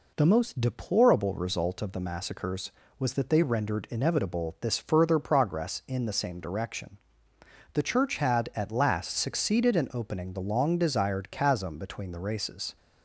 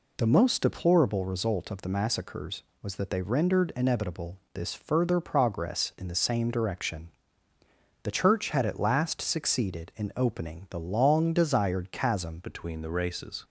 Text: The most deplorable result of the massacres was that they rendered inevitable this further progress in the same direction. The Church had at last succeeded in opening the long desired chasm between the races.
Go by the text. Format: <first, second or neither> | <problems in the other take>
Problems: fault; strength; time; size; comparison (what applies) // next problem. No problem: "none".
first | pauses between "inevitable" and "this"; slight; at 4.3 s; 0.16 s long // changes voice at "between"; from 12.4 s on; 1.0 s long